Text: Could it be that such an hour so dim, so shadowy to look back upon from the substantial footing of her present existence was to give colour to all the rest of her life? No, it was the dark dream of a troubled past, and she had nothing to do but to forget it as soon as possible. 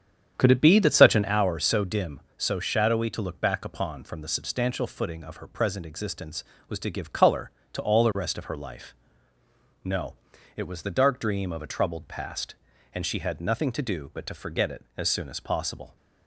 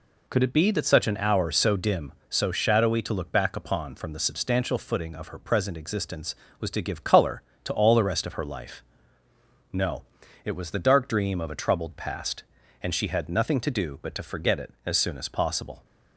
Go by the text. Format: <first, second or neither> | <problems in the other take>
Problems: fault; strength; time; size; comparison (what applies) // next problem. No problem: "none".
second | starts louder than the rest; strong; until 1.5 s; 8.5 dB